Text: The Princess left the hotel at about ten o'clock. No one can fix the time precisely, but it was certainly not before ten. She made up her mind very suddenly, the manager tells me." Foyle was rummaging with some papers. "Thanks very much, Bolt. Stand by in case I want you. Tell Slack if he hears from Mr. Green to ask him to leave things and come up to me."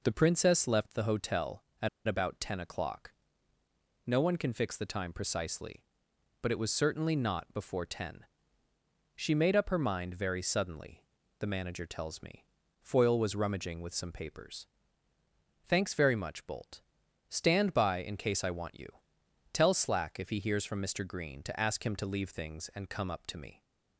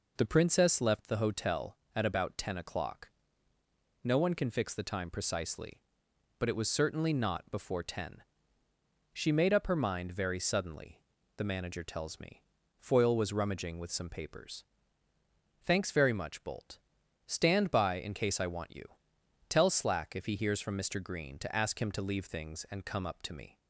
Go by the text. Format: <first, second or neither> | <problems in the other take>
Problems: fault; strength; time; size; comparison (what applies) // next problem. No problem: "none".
second | pauses between "at" and "about"; slight; at 1.8 s; 0.19 s long